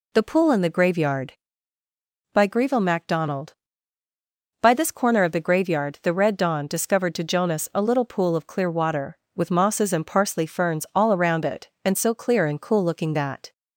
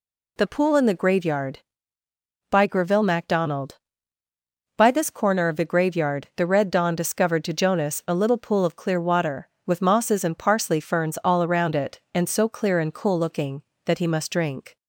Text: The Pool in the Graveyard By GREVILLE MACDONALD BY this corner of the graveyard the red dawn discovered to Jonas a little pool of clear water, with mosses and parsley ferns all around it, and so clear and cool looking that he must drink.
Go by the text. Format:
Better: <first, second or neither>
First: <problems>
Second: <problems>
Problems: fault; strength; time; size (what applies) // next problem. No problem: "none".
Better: second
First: stops before "he must drink"; at 13.5 s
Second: none